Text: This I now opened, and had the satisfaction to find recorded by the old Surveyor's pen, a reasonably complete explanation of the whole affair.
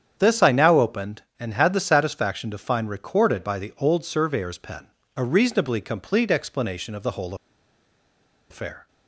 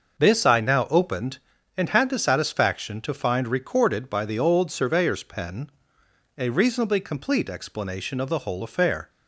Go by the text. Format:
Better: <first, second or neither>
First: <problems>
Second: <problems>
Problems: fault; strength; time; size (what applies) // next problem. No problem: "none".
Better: second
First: starts louder than the rest; strong; until 1.1 s; 8 dB // pauses between "whole" and "affair"; at 7.3 s; 1.1 s long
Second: starts louder than the rest; until 1.2 s; 6 dB